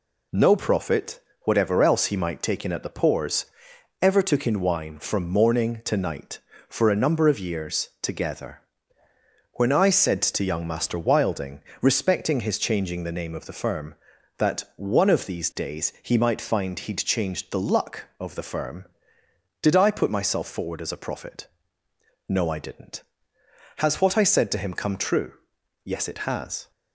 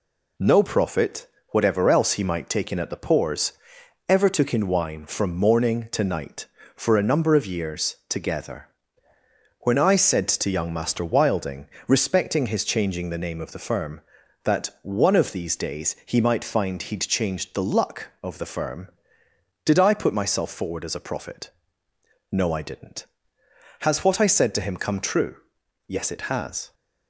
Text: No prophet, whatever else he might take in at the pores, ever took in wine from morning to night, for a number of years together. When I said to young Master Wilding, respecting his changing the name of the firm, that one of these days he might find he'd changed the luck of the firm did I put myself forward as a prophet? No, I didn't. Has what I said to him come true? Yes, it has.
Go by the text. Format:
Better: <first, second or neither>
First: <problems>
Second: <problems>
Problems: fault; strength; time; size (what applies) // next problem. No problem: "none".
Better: neither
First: none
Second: none